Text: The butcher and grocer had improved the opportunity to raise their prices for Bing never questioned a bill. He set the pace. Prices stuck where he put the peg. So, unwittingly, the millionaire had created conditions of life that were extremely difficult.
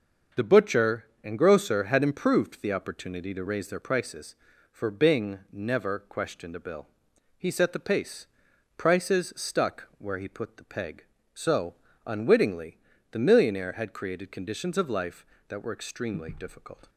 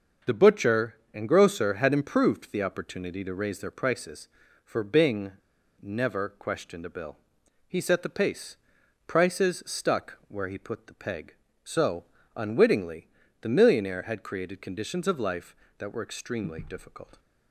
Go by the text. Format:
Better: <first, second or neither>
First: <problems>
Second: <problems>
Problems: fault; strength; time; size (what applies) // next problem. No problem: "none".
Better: first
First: starts louder than the rest; until 1.5 s; 6.5 dB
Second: starts louder than the rest; until 1.4 s; 6 dB // pauses between "Bing" and "never"; noticeable; at 5.3 s; 0.49 s long